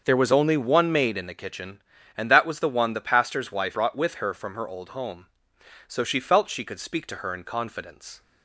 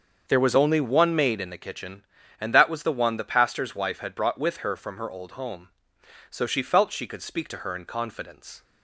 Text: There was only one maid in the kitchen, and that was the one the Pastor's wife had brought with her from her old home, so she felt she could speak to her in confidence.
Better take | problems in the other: second | starts louder than the rest; until 1.0 s; 6.5 dB; also in the second // skips "had"; at 3.7 s

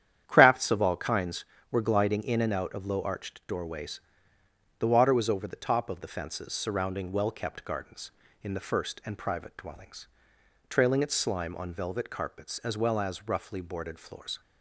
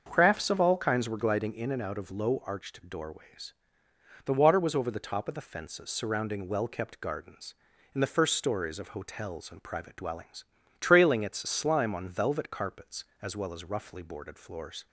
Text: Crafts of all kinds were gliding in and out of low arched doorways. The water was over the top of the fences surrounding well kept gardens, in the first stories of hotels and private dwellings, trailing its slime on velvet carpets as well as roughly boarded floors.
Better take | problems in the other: second | starts louder than the rest; strong; until 1.2 s; 10 dB; also in the second // skips "stories of hotels"; at 9.0 s

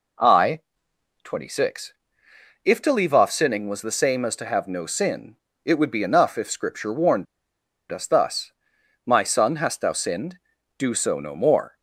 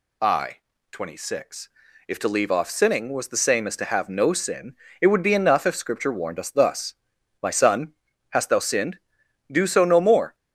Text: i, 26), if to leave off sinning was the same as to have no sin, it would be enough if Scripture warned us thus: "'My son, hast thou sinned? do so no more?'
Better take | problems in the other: second | pauses between "warned" and "us"; noticeable; at 7.2 s; 0.65 s long

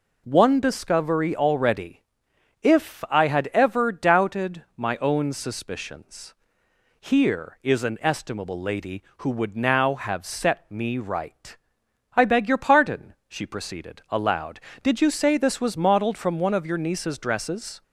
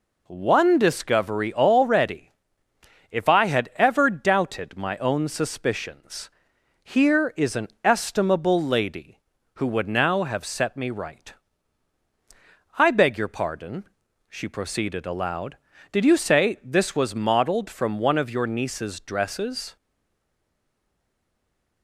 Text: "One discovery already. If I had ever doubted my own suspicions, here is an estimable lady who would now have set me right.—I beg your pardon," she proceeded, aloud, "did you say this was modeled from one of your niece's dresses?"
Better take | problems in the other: first | pauses between "an" and "estimable"; slight; at 7.6 s; 0.16 s long // stays silent after the last word; noticeable; from 19.7 s on; 2.1 s long

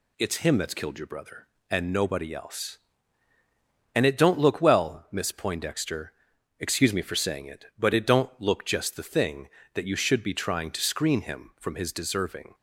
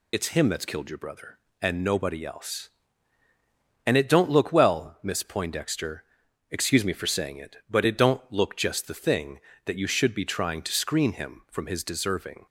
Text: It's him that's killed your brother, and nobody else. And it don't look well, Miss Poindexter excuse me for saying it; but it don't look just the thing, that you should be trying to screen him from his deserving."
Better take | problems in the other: first | loses the start of "It's"; at 0.1 s; 60 ms // pauses between "Poindexter" and "excuse"; noticeable; at 6.0 s; 0.48 s long; noticeable in the first

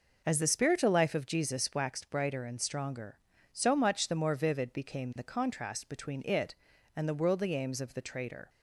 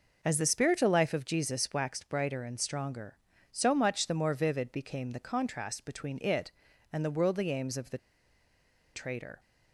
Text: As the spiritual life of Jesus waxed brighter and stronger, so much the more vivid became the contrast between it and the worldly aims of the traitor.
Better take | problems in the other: first | pauses between "the" and "traitor"; noticeable; at 7.9 s; 0.96 s long

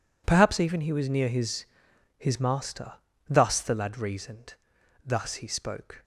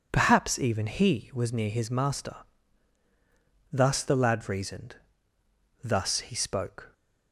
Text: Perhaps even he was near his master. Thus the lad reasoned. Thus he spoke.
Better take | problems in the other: second | says "his" twice; at 2.1 s

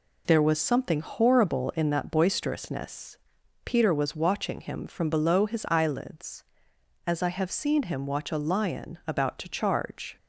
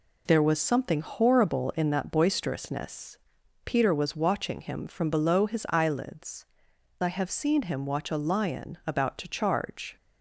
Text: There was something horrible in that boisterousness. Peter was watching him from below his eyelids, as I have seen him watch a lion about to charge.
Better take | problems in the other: first | skips "as"; at 6.7 s

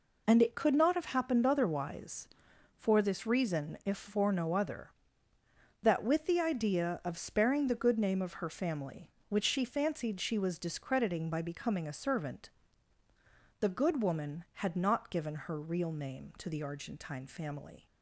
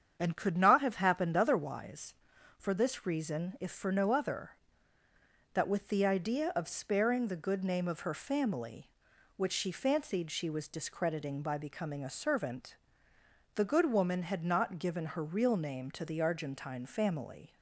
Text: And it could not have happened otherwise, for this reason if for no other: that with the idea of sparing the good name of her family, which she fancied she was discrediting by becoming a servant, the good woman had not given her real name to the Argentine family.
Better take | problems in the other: first | starts louder than the rest; strong; until 1.1 s; 7.5 dB // skips "it"; at 0.3 s

